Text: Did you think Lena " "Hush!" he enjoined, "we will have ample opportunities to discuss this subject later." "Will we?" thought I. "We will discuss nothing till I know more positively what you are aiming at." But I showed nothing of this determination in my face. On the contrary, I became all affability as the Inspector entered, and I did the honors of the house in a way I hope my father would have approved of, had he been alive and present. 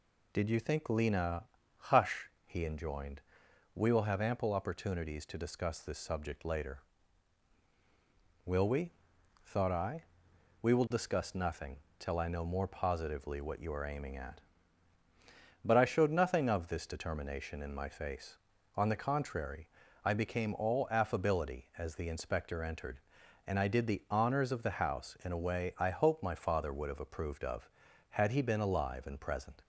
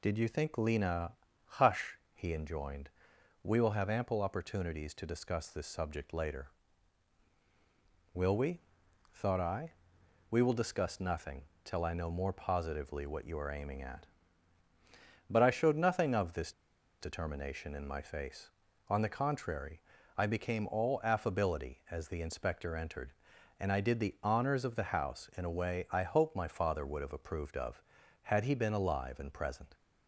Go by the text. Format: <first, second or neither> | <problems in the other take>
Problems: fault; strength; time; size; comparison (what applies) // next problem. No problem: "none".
first | pauses between "nothing" and "till"; slight; at 11.4 s; 0.20 s long; slight in the first // pauses between "this" and "determination"; noticeable; at 16.5 s; 0.48 s long